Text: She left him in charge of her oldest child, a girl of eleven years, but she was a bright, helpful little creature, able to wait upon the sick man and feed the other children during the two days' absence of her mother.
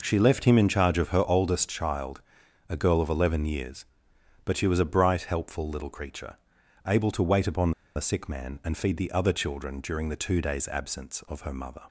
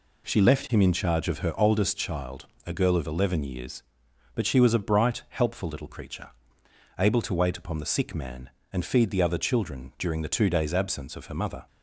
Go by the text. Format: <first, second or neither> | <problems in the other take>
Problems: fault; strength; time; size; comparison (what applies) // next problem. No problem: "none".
second | pauses between "upon" and "the"; slight; at 7.7 s; 0.24 s long